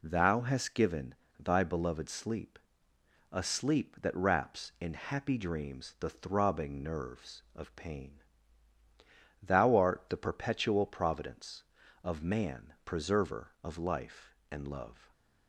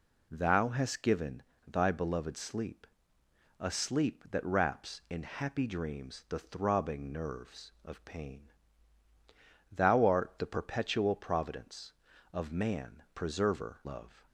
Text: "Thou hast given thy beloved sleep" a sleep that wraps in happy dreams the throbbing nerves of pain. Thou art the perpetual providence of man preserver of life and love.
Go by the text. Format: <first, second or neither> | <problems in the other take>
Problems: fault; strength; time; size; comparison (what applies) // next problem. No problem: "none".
first | pauses between "given" and "thy"; slight; at 1.4 s; 0.26 s long; slight in the first // pauses between "sleep" and "a"; noticeable; at 2.8 s; 0.74 s long; noticeable in the first // skips "of life and"; at 13.8 s